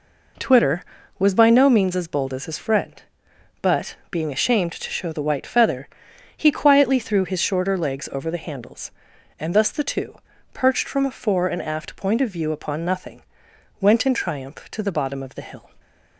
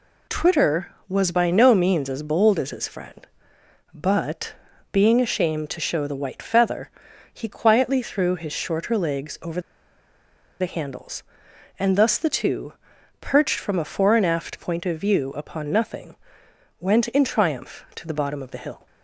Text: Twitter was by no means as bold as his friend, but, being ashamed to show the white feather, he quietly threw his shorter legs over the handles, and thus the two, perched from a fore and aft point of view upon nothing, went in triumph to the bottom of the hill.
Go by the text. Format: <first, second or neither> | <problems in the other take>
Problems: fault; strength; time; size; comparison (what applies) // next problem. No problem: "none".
first | pauses between "over" and "the"; at 9.5 s; 1.0 s long